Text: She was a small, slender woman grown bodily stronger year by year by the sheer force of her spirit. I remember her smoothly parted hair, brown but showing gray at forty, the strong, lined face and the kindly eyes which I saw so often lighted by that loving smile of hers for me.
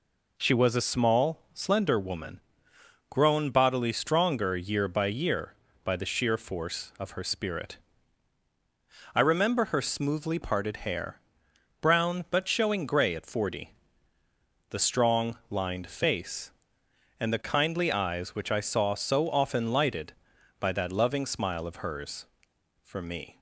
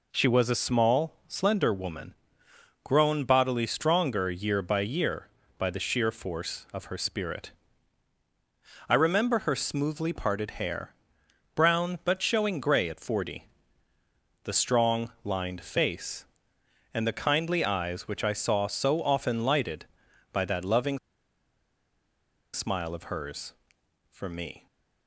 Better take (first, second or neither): first